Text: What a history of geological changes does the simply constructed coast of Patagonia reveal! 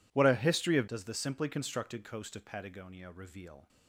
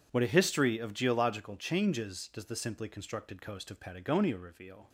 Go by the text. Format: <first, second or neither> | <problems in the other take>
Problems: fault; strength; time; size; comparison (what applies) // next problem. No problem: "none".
second | skips "geological changes"; at 0.8 s